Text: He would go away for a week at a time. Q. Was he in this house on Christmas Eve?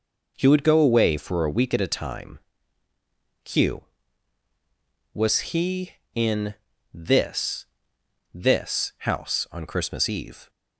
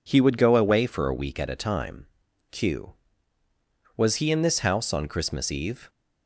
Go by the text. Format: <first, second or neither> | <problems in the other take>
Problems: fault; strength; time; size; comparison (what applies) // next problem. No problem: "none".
second | pauses between "in" and "this"; at 6.5 s; 0.38 s long // says "this" twice; at 8.3 s